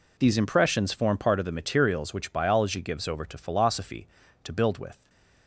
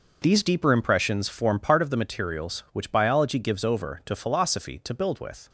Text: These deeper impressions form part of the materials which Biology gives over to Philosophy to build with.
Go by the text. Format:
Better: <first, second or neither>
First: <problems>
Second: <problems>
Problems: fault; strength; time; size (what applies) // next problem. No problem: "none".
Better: second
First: skips "deeper"; at 0.3 s // stays silent after the last word; slight; from 4.9 s on; 0.5 s long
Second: none